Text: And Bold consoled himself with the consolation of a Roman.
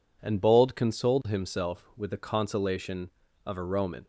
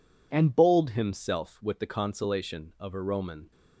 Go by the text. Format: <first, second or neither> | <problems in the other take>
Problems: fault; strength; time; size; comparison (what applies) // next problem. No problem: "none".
first | skips "consoled"; at 0.9 s